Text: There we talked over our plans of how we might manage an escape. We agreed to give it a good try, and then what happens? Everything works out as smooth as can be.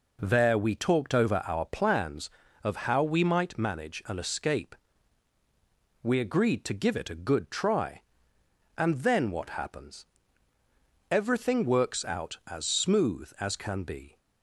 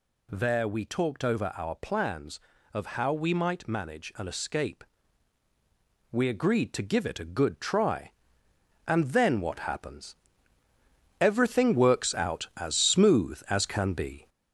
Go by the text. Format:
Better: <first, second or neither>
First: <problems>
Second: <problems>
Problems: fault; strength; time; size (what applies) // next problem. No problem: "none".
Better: first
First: none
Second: gets louder; noticeable; throughout; 4.5 dB